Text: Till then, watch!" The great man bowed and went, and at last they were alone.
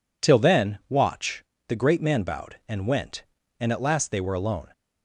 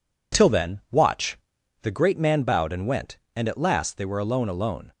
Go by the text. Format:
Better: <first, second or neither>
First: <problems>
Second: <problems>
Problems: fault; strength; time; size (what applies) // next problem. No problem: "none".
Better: first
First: none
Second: says "alone" twice; at 4.4 s